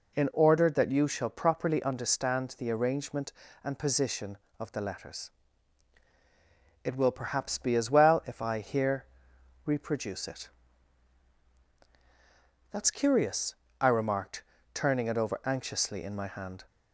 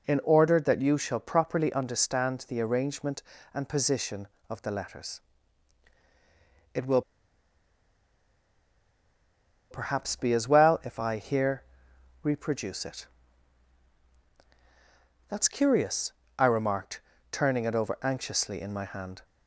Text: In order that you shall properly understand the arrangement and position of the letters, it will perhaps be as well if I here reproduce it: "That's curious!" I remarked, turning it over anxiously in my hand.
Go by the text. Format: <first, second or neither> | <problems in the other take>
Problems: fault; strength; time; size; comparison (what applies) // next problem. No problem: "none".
first | pauses between "will" and "perhaps"; strong; at 7.0 s; 2.7 s long // pauses between "here" and "reproduce"; noticeable; at 11.6 s; 0.60 s long; noticeable in the first